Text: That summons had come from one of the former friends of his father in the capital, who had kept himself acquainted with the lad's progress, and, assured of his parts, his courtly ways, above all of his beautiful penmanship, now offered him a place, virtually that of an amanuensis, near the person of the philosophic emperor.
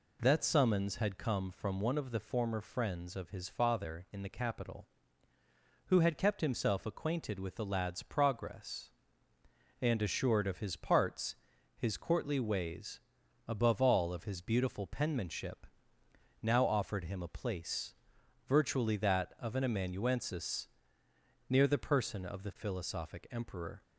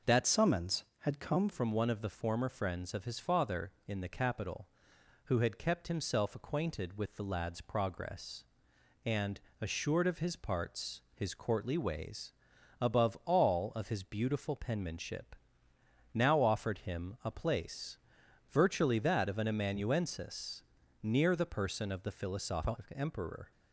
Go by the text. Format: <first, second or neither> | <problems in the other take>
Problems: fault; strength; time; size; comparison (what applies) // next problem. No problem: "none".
first | changes voice from "summons" to "come"; from 0.2 to 1.4 s; 1.2 s long